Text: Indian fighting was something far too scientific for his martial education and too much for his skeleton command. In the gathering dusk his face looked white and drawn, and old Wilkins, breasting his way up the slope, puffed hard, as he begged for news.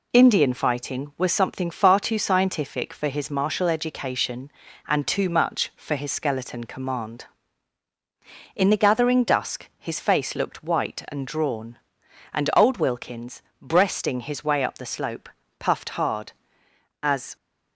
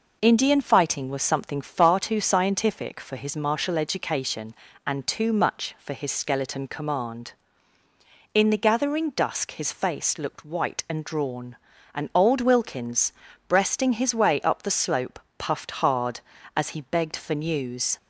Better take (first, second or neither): second